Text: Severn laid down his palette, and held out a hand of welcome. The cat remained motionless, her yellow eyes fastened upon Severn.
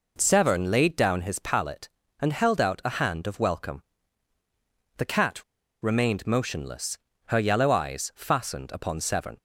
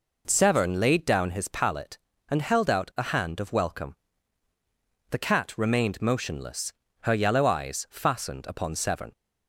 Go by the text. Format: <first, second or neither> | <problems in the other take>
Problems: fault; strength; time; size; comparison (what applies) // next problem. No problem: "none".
second | pauses between "cat" and "remained"; at 5.4 s; 0.39 s long